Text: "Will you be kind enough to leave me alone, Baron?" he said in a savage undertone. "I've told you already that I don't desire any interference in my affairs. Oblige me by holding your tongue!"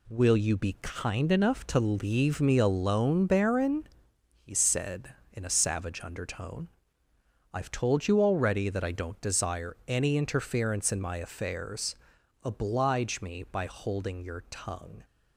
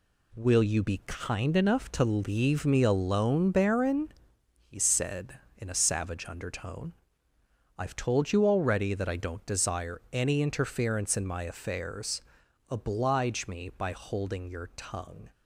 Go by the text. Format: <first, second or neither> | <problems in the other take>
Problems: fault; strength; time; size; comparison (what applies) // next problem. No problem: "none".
neither | none